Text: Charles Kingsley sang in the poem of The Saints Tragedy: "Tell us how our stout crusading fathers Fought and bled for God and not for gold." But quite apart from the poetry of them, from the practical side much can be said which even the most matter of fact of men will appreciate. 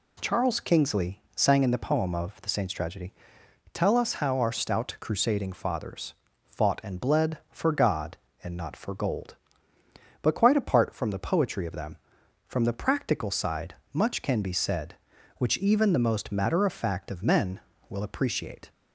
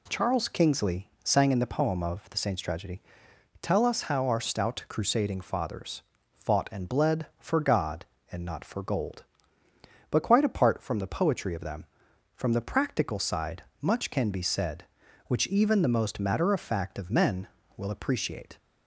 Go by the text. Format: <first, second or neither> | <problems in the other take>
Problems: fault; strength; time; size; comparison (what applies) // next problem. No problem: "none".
neither | pauses between "Kingsley" and "sang"; slight; the same in both // pauses between "fathers" and "Fought"; slight; the same in both // pauses between "side" and "much"; slight; the same in both